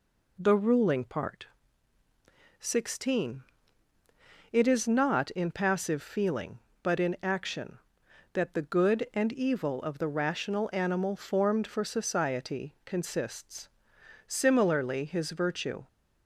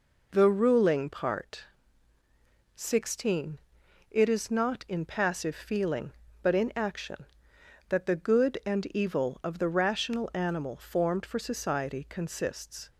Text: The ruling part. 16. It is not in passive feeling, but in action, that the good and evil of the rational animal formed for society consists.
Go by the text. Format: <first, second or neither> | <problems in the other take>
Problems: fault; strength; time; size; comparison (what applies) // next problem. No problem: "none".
second | goes on to say "Similarly his virtue"; from 14.2 s on; 1.6 s long